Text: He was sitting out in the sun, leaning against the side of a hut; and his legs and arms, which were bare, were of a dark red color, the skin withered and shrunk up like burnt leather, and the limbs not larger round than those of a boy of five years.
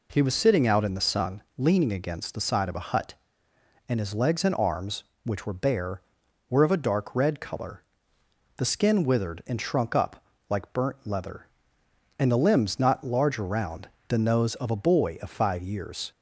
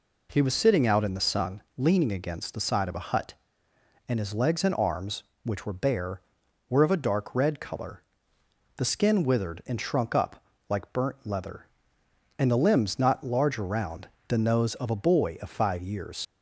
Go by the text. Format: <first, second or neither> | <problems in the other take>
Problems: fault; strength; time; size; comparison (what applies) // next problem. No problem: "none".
first | pauses between "up" and "like"; slight; at 10.4 s; 0.28 s long; slight in the first // leaves "years" unfinished; at 16.2 s; 55 ms